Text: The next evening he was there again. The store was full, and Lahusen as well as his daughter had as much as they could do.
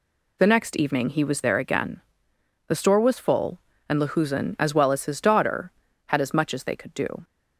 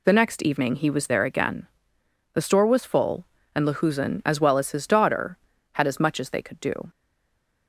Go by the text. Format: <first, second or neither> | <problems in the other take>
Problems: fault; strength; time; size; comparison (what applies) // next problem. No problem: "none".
first | stays silent after the last word; slight; from 6.8 s on; 0.8 s long